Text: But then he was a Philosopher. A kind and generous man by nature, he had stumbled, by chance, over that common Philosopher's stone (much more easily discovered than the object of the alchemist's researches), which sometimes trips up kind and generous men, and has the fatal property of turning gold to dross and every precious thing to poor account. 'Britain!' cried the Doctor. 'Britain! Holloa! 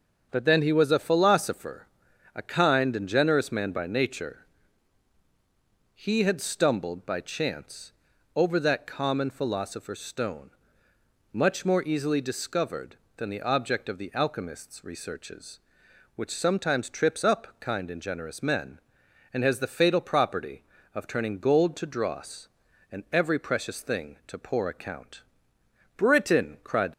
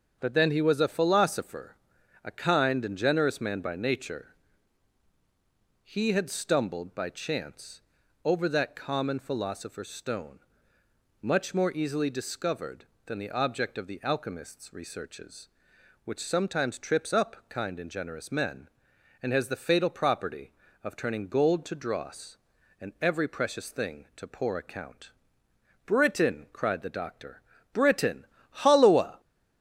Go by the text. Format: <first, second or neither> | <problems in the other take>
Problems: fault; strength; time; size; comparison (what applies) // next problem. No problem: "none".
second | starts louder than the rest; until 1.3 s; 7 dB; also in the second // stops before "the Doctor Britain Holloa"; at 26.9 s